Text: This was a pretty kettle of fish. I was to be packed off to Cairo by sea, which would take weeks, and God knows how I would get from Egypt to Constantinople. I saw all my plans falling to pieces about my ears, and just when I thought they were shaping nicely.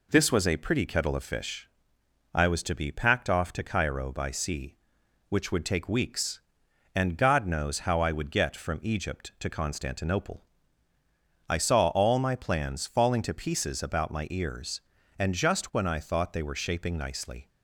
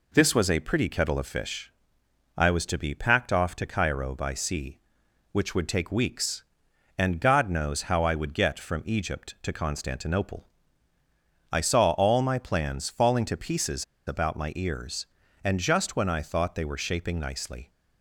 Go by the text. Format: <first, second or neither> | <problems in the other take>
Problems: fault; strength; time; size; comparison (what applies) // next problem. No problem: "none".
first | pauses between "pieces" and "about"; slight; at 13.8 s; 0.23 s long